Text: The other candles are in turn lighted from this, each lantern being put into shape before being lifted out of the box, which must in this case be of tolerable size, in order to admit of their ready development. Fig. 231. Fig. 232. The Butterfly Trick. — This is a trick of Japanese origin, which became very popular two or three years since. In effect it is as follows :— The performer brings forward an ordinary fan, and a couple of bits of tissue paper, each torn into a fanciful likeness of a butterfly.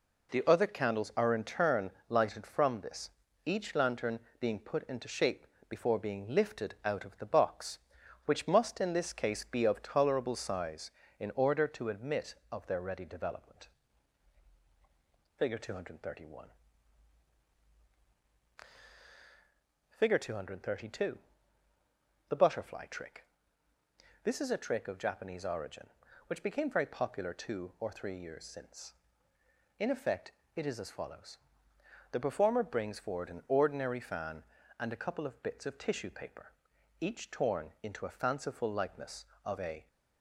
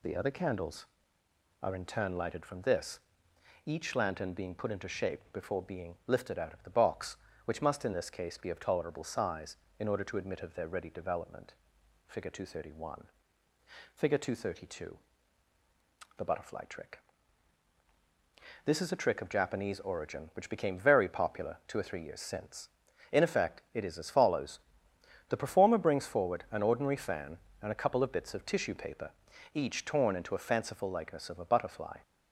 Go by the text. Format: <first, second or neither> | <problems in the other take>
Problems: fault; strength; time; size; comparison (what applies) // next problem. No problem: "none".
second | pauses between "turn" and "lighted"; slight; at 1.9 s; 0.18 s long // pauses between "lantern" and "being"; slight; at 4.2 s; 0.18 s long // pauses between "shape" and "before"; slight; at 5.4 s; 0.22 s long // pauses between "effect" and "it"; slight; at 30.3 s; 0.24 s long // stops before "butterfly"; at 39.8 s